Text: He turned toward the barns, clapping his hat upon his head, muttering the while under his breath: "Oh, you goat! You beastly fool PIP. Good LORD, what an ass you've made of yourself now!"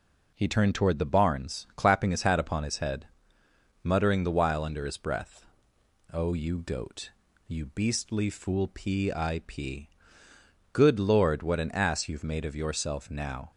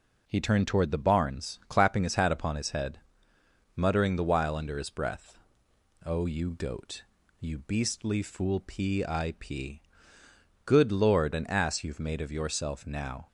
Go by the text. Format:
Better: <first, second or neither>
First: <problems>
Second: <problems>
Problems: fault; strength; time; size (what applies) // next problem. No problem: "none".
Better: first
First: none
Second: skips "what"; at 11.3 s